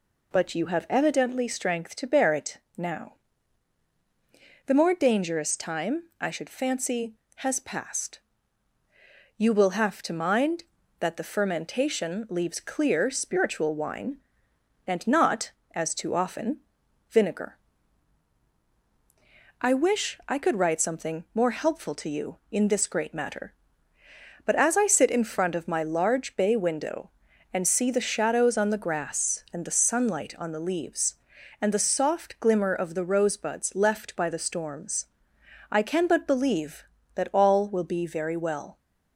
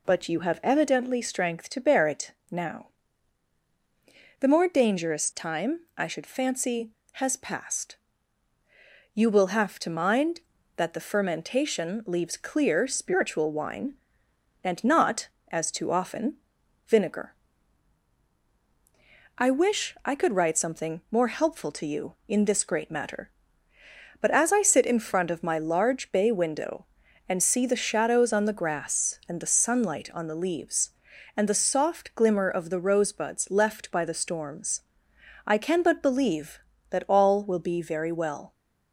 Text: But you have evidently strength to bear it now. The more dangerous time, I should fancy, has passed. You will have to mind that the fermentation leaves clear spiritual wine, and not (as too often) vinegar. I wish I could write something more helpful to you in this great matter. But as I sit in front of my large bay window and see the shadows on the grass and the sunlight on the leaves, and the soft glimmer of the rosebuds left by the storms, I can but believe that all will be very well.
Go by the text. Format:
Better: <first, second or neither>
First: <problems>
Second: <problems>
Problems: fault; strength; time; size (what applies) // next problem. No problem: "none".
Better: neither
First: pauses between "it" and "now"; slight; at 2.5 s; 0.18 s long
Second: pauses between "it" and "now"; slight; at 2.3 s; 0.18 s long